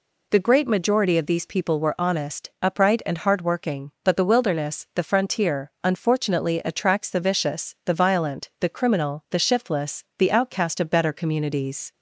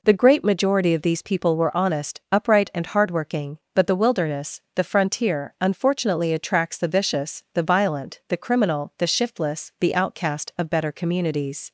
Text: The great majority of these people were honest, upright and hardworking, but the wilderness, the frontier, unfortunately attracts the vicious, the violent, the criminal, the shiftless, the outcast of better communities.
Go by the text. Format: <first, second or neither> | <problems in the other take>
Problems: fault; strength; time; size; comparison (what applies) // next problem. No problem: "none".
neither | none